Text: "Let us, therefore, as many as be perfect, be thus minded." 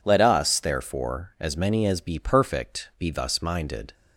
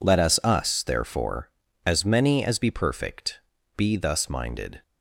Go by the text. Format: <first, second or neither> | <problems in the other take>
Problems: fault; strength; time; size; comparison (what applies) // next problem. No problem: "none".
first | says "us" twice; at 0.4 s